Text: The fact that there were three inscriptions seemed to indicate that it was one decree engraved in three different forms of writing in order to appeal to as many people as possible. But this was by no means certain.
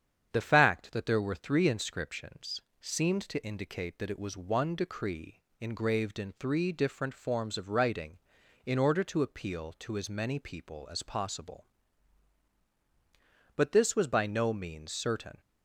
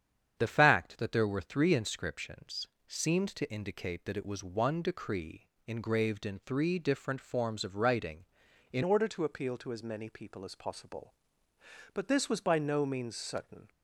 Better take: first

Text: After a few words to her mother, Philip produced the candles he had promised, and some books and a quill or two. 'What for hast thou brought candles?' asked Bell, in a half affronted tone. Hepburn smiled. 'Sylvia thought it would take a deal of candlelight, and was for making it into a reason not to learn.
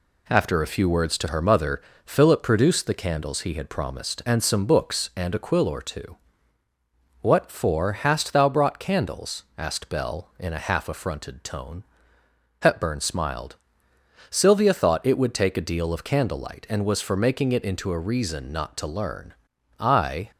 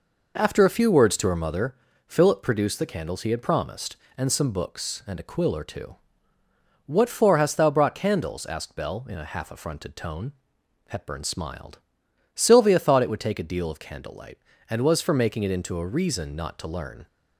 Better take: second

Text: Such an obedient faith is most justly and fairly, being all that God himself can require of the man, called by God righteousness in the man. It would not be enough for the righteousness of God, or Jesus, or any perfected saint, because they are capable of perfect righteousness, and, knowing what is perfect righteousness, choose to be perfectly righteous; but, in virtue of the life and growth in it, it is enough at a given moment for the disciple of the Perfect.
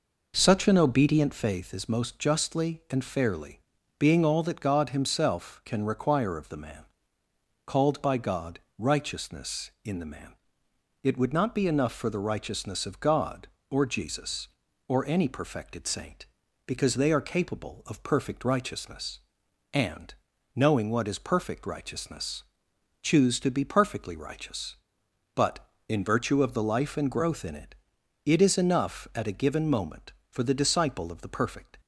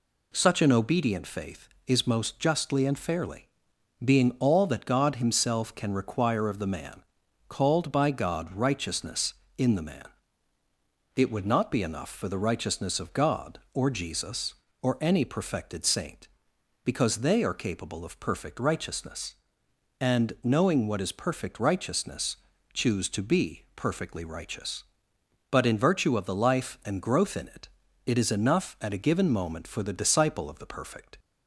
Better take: second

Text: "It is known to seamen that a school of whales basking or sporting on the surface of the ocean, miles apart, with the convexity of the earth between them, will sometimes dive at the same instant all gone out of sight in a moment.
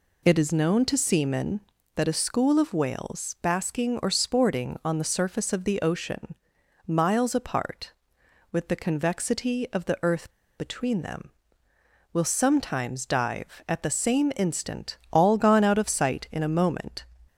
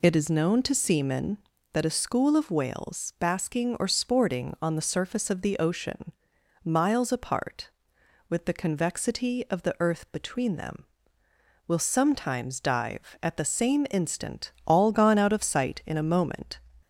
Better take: second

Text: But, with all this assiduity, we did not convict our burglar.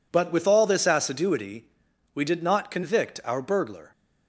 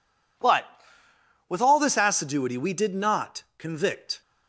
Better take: first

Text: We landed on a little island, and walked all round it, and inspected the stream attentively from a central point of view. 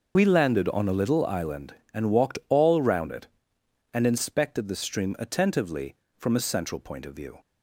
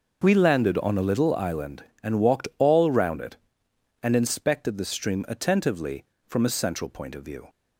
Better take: second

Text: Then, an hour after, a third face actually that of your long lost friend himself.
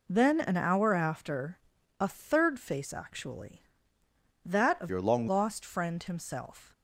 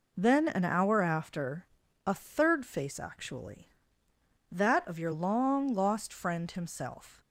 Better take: second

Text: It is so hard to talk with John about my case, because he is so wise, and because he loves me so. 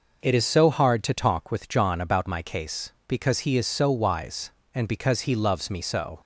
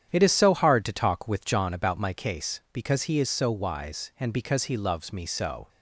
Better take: first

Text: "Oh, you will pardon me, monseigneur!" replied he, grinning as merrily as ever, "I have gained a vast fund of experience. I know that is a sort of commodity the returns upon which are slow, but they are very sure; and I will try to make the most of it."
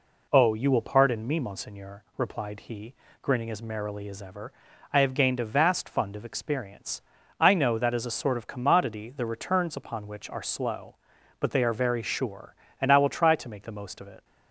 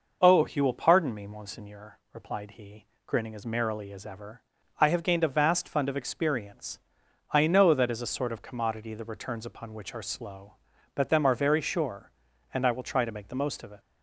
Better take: first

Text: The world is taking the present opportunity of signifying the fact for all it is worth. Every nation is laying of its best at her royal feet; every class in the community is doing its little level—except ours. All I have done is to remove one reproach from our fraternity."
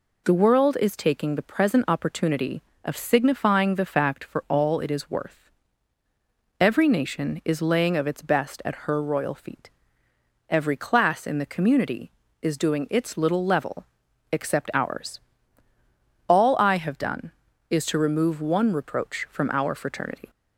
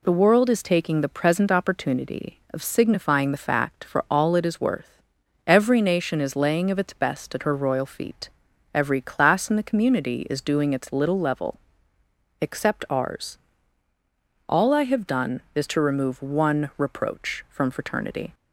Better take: first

